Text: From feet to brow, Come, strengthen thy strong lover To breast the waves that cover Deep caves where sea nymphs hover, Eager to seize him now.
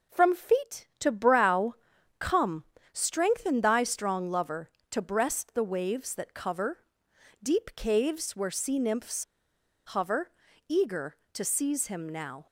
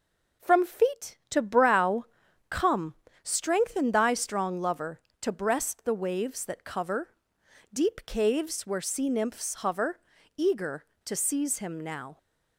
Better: second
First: pauses between "cover" and "Deep"; noticeable; at 6.7 s; 0.64 s long // pauses between "nymphs" and "hover"; noticeable; at 9.2 s; 0.61 s long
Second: pauses between "cover" and "Deep"; noticeable; at 7.0 s; 0.64 s long

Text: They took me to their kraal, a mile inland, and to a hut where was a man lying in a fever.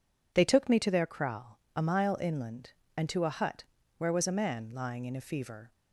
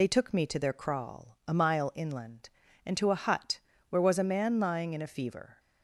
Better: first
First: pauses between "hut" and "where"; slight; at 3.6 s; 0.34 s long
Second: loses the start of "They"; at 0.0 s; 50 ms // pauses between "hut" and "where"; slight; at 3.6 s; 0.30 s long

